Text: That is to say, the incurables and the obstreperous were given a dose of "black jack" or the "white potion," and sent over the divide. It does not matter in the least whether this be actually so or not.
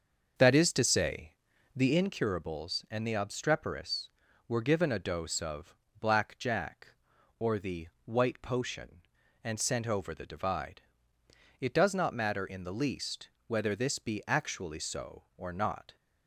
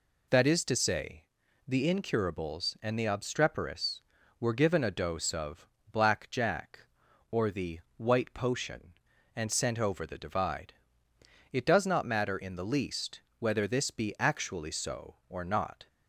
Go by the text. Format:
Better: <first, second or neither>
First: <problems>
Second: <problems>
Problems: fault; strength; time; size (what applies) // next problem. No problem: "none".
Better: second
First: starts louder than the rest; until 2.2 s; 6.5 dB // pauses between "of" and "black"; slight; at 5.7 s; 0.24 s long // pauses between "the" and "white"; slight; at 7.8 s; 0.18 s long // pauses between "least" and "whether"; slight; at 13.2 s; 0.18 s long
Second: pauses between "of" and "black"; slight; at 5.6 s; 0.24 s long // pauses between "the" and "white"; slight; at 7.7 s; 0.18 s long // pauses between "least" and "whether"; slight; at 13.2 s; 0.18 s long